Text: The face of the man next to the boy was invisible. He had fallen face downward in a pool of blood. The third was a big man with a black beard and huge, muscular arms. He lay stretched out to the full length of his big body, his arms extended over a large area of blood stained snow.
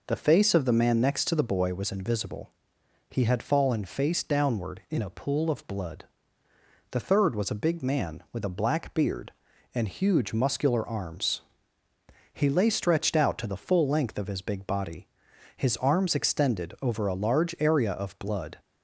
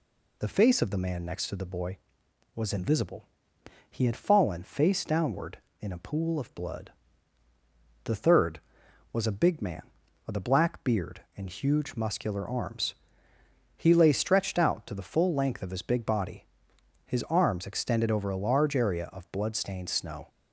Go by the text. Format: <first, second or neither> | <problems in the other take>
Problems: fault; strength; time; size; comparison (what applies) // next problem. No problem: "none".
second | stops before "stained snow"; at 18.5 s